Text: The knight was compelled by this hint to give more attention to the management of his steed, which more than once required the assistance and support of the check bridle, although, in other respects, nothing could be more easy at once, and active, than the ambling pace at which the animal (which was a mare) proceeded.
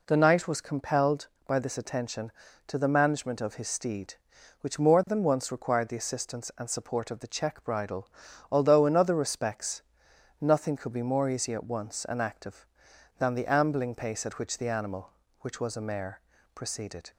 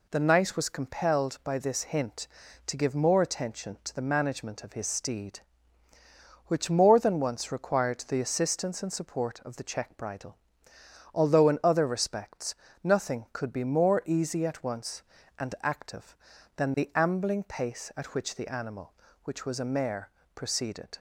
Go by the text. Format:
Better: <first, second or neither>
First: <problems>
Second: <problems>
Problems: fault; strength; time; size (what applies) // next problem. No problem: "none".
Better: second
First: skips "hint to give more"; at 1.7 s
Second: none